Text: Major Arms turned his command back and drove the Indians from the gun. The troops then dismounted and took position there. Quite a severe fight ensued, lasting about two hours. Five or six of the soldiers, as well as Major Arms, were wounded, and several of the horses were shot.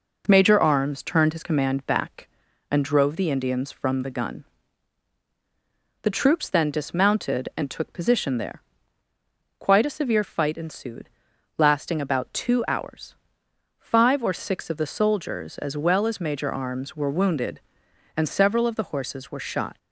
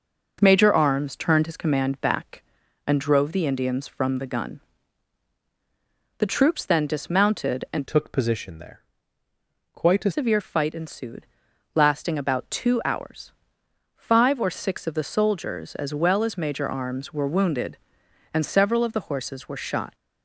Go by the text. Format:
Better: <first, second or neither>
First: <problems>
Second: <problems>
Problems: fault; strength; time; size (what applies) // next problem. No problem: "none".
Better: first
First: none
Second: changes voice from "took" to "a"; from 7.8 to 10.1 s; 2.3 s long